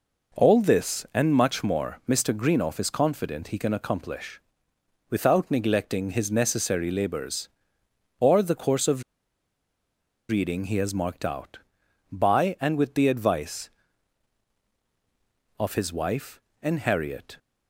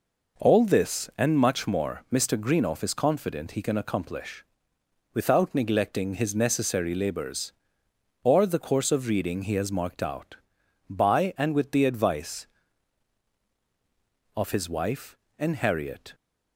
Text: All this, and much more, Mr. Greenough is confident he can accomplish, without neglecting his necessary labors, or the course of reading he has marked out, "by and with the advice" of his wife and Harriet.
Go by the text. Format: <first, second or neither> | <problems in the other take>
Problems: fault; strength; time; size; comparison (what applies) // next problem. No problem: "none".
second | pauses between "of" and "reading"; strong; at 9.0 s; 1.2 s long